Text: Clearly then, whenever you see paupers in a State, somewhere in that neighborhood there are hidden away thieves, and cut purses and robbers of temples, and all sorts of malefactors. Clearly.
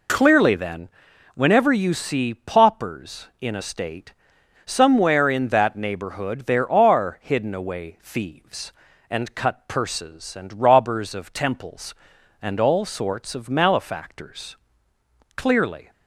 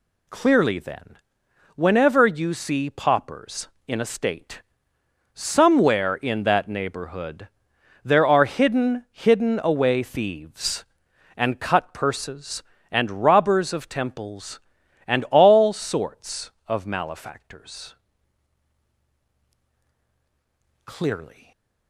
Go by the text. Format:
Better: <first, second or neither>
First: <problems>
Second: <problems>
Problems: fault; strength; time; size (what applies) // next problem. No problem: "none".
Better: first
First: none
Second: pauses between "neighborhood" and "there"; noticeable; at 7.4 s; 0.56 s long // says "hidden" twice; at 9.0 s // stays silent after the last word; slight; from 21.3 s on; 0.5 s long